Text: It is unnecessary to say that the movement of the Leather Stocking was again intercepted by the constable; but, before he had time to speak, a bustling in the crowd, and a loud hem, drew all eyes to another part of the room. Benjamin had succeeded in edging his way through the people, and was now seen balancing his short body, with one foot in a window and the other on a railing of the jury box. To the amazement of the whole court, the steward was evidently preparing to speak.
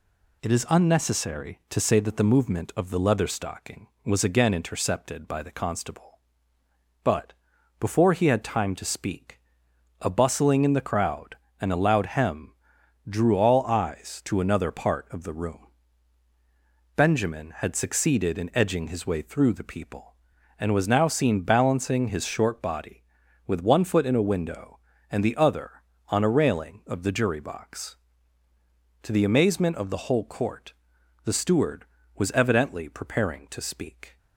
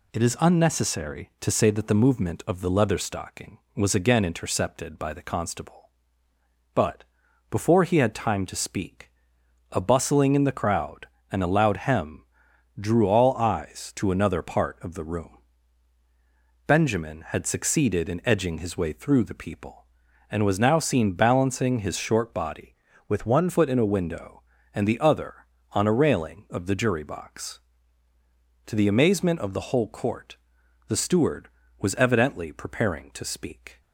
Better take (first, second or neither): first